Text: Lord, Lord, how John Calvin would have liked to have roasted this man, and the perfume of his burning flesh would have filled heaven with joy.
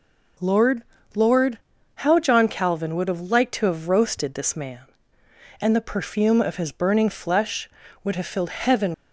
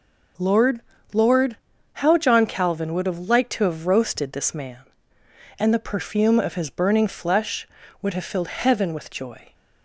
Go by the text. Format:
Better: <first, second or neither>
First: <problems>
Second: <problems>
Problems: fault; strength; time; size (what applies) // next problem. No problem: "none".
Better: second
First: stops before "with joy"; at 8.9 s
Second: none